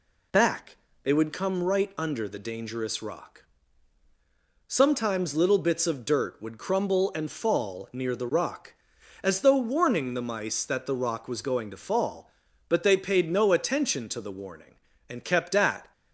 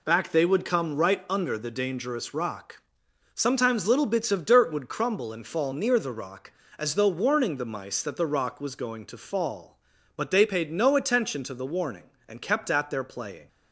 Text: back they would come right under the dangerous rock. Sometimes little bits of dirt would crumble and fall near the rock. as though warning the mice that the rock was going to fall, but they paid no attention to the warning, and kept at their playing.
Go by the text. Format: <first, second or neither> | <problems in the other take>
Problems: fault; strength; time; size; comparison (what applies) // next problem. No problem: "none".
second | pauses between "back" and "they"; slight; at 0.7 s; 0.26 s long // stops before "their playing"; at 15.9 s